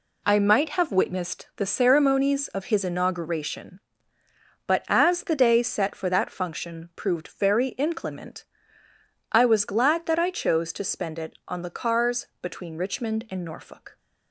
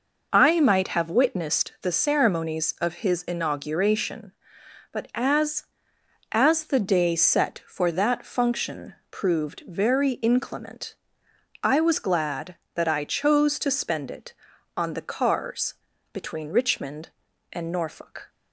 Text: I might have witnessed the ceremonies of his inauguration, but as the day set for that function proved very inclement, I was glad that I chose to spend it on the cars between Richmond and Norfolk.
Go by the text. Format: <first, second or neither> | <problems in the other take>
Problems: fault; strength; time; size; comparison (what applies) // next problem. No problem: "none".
first | says "as" twice; at 6.3 s // pauses between "function" and "proved"; slight; at 8.9 s; 0.16 s long // pauses between "cars" and "between"; at 15.7 s; 0.38 s long; slight in the first